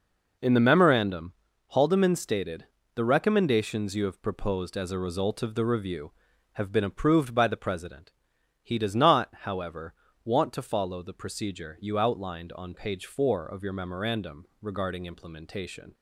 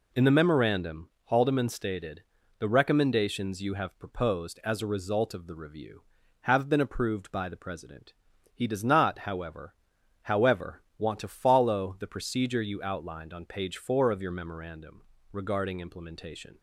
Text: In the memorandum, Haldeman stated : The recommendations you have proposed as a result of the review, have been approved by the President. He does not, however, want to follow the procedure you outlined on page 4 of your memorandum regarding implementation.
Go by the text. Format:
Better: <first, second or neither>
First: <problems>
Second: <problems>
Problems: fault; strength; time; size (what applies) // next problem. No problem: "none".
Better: first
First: pauses between "memorandum" and "regarding"; slight; at 14.4 s; 0.16 s long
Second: says "however" twice; at 10.2 s // pauses between "memorandum" and "regarding"; slight; at 15.0 s; 0.30 s long